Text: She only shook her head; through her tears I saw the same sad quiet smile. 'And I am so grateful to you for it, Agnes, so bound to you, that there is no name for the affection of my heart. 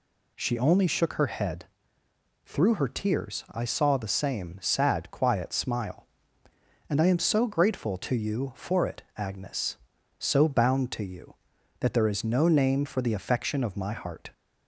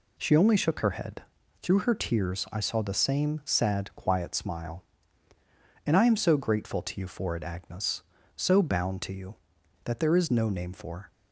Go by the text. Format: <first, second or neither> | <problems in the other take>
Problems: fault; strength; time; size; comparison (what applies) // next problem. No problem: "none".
first | stops before "the affection of my heart"; at 11.1 s